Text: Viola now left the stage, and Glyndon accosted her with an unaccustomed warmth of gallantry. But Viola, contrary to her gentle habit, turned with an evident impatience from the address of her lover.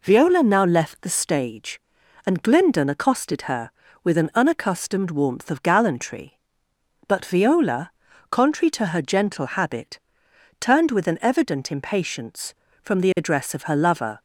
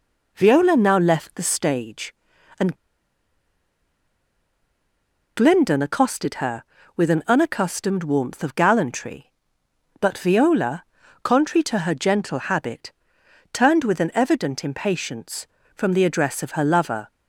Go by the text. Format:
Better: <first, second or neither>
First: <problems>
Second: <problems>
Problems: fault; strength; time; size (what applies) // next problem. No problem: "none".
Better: first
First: none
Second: pauses between "and" and "Glyndon"; strong; at 2.7 s; 2.6 s long